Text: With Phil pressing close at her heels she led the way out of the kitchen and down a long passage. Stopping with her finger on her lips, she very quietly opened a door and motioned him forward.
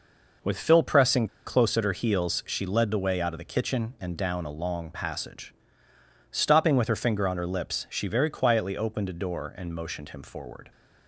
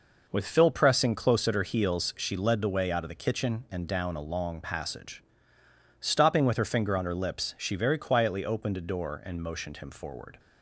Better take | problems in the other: second | pauses between "pressing" and "close"; slight; at 1.2 s; 0.19 s long

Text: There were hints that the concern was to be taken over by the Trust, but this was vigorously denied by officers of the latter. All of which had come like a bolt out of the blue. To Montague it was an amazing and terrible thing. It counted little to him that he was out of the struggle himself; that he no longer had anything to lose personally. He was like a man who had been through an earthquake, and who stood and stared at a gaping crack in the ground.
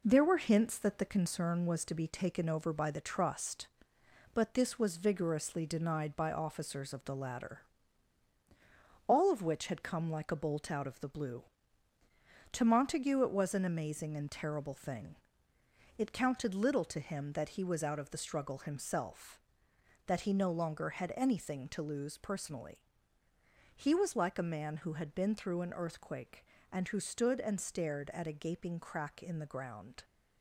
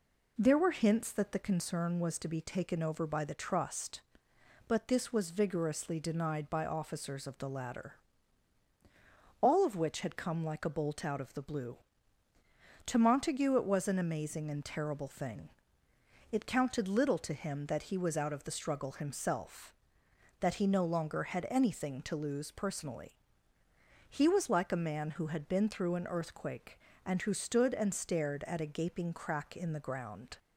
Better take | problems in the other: second | gets quieter; noticeable; throughout; 5.5 dB

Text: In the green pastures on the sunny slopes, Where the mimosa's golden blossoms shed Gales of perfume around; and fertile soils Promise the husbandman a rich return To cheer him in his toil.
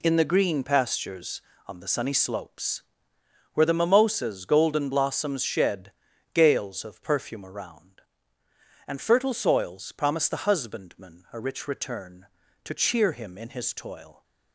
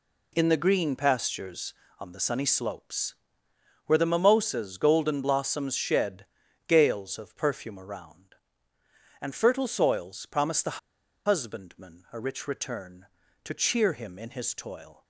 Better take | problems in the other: first | pauses between "shed" and "Gales"; at 6.2 s; 0.40 s long; also in the first // pauses between "the" and "husbandman"; noticeable; at 10.7 s; 0.48 s long

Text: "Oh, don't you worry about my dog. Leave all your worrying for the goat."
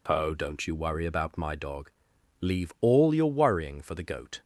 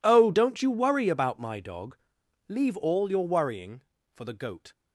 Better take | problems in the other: neither | none

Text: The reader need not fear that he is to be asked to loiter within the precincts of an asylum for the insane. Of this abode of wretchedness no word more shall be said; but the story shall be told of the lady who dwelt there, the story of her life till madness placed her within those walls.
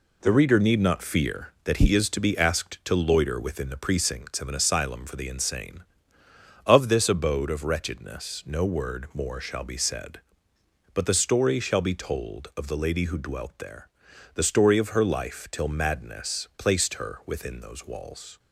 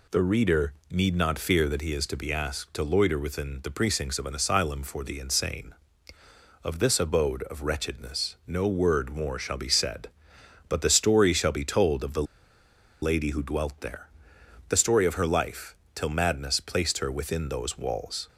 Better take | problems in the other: first | pauses between "reader" and "need"; slight; at 0.7 s; 0.18 s long // pauses between "the" and "lady"; noticeable; at 12.2 s; 0.78 s long // pauses between "life" and "till"; slight; at 15.7 s; 0.20 s long

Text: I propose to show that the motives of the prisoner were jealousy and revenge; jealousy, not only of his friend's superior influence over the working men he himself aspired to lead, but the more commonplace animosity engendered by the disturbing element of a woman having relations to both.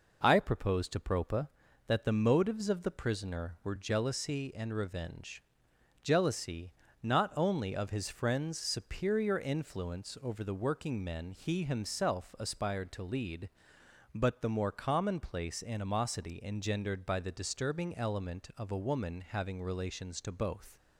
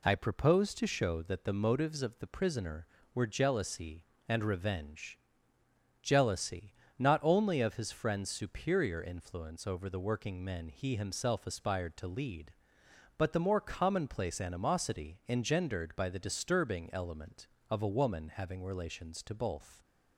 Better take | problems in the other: second | says "propa" for "show"; at 0.9 s

